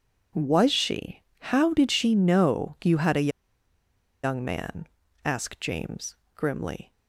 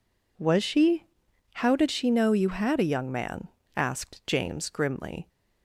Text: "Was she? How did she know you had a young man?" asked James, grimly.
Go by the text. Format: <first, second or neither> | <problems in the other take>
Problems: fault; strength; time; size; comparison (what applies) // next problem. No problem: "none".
second | pauses between "a" and "young"; noticeable; at 3.2 s; 0.94 s long